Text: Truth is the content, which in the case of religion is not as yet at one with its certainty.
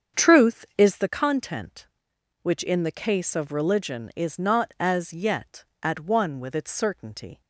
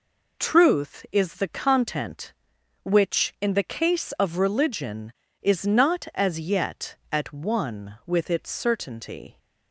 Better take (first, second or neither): second